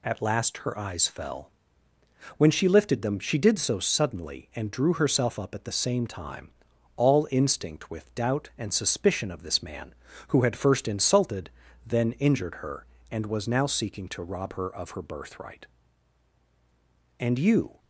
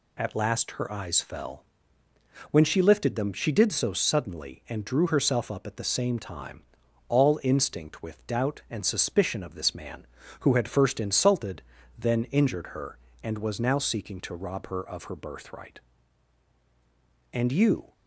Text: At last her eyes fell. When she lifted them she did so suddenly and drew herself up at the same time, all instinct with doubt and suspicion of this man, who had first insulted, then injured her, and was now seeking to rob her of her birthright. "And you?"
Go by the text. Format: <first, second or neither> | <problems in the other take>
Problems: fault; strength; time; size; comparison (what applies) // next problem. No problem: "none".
neither | none